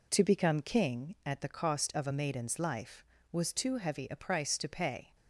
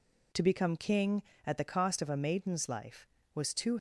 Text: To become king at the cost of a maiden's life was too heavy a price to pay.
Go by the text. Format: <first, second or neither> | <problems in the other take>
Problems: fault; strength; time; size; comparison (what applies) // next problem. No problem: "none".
first | stops before "heavy a price to pay"; at 3.7 s